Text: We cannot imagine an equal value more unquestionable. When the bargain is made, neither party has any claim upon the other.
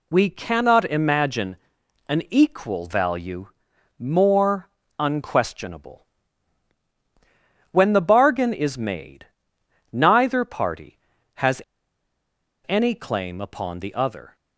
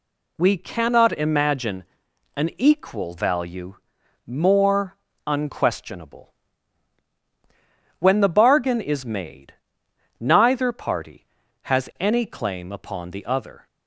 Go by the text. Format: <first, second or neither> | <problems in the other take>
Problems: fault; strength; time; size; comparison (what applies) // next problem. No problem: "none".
second | pauses between "imagine" and "an"; noticeable; at 1.5 s; 0.52 s long; noticeable in the second // pauses between "value" and "more"; noticeable; at 3.4 s; 0.50 s long; noticeable in the second // pauses between "more" and "unquestionable"; slight; at 4.6 s; 0.30 s long; slight in the second // pauses between "has" and "any"; at 11.6 s; 1.0 s long